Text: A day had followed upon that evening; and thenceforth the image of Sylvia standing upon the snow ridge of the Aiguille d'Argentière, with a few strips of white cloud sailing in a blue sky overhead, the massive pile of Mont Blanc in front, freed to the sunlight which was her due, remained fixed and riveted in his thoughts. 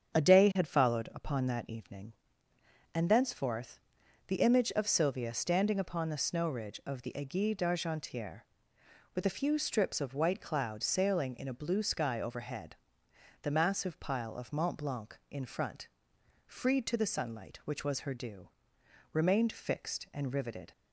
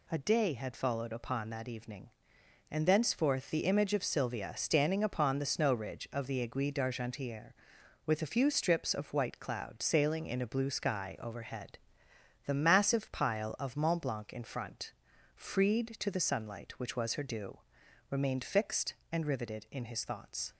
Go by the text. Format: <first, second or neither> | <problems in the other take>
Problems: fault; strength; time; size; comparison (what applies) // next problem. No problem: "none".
second | starts louder than the rest; strong; until 1.2 s; 7.5 dB // pauses between "thenceforth" and "the"; noticeable; at 3.7 s; 0.48 s long // stops before "in his thoughts"; at 20.7 s